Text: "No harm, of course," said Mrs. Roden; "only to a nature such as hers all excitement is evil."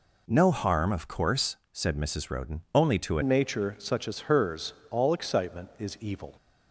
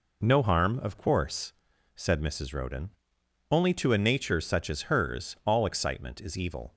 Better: second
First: changes voice at "nature"; from 3.2 s on; 3.1 s long // pauses between "hers" and "all"; slight; at 4.7 s; 0.16 s long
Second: none

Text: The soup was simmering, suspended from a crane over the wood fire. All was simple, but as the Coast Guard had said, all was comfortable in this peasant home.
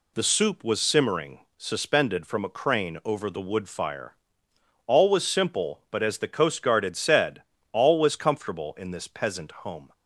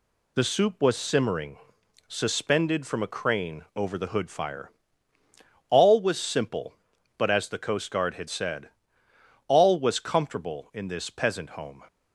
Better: first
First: none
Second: says "hood" for "wood"; at 4.0 s

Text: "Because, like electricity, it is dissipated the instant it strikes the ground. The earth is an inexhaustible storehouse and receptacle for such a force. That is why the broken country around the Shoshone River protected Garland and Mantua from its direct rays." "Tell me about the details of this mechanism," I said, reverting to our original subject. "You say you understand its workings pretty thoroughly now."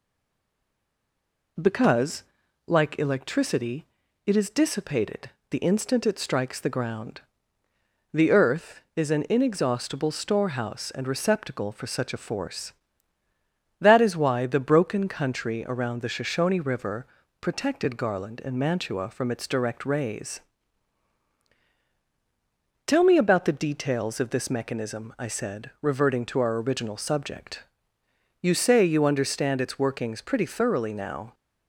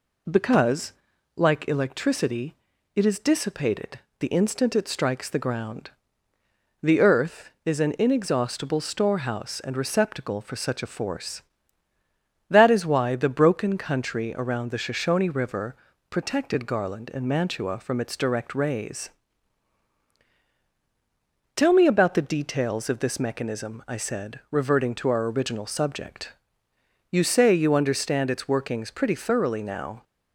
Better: second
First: stays silent before the first word; noticeable; until 1.5 s; 1.5 s long // pauses between "dissipated" and "the"; slight; at 5.2 s; 0.20 s long // pauses between "River" and "protected"; slight; at 17.0 s; 0.34 s long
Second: pauses between "dissipated" and "the"; slight; at 3.9 s; 0.20 s long // pauses between "River" and "protected"; slight; at 15.7 s; 0.34 s long

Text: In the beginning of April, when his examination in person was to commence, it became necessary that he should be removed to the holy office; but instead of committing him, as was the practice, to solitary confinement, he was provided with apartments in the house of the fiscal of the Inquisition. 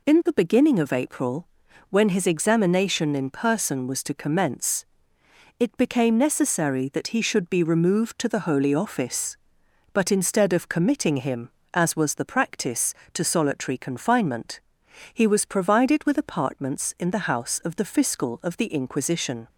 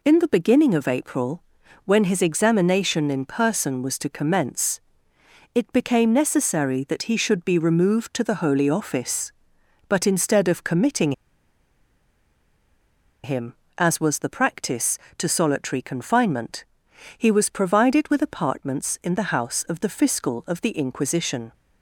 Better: first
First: none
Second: pauses between "committing" and "him"; strong; at 11.1 s; 2.1 s long

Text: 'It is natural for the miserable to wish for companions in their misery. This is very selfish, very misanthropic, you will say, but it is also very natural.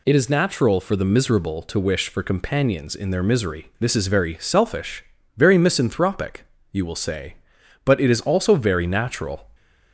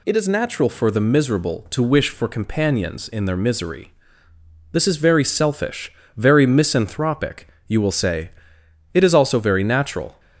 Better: first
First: none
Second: skips "but"; at 8.6 s

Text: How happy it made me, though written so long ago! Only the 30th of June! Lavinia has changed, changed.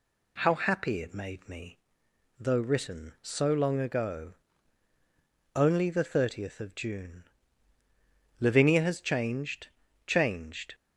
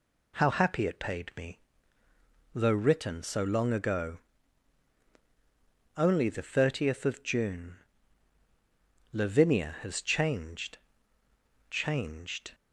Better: first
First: none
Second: says "paid" for "made"; at 0.9 s

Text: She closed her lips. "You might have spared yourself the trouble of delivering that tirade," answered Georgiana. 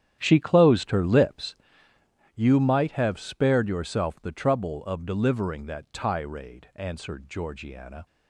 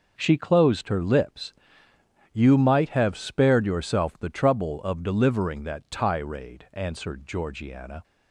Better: second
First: starts louder than the rest; strong; until 1.6 s; 10 dB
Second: none

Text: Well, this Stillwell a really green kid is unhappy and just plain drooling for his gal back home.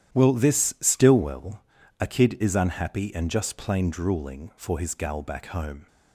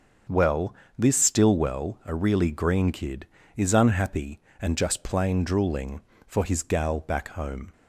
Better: second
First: starts louder than the rest; strong; until 1.2 s; 11 dB // pauses between "Stillwell" and "a"; at 1.6 s; 0.40 s long // skips "really green"; at 2.0 s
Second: starts louder than the rest; until 1.5 s; 7 dB

